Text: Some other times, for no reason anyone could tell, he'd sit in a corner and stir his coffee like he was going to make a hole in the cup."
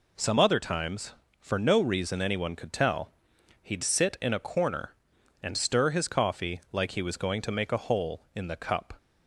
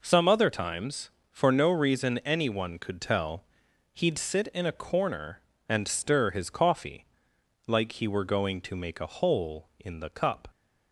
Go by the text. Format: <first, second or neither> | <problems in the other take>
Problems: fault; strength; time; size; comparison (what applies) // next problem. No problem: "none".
first | pauses between "coffee" and "like"; noticeable; at 7.0 s; 0.62 s long // says "were" for "was"; at 8.0 s